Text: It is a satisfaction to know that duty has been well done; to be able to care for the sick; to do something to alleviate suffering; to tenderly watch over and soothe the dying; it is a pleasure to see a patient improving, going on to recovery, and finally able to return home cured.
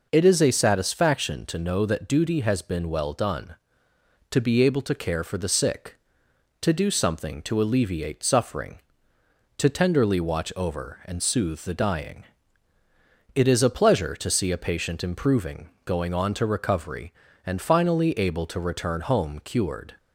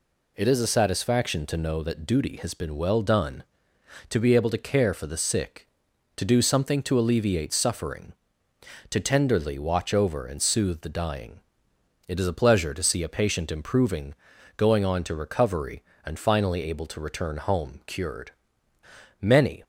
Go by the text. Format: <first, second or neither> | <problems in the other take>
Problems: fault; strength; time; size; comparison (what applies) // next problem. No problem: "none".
first | goes on to say "Many"; slight; from 19.2 s on; 0.42 s long